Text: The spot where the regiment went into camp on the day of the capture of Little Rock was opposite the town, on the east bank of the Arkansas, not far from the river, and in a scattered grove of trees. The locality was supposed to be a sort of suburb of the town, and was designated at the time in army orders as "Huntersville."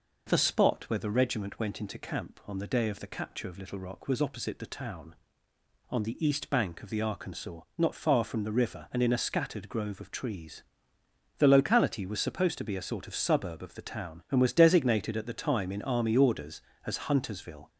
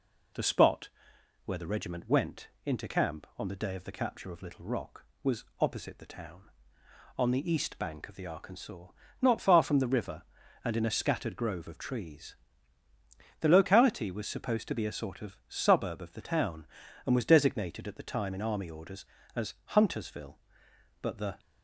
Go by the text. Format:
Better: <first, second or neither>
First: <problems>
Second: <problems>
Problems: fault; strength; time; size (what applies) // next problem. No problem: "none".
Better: first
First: none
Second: pauses between "spot" and "where"; noticeable; at 0.8 s; 0.56 s long // pauses between "went" and "into"; slight; at 2.4 s; 0.18 s long // goes on to say "But the"; slight; from 21.0 s on; 0.38 s long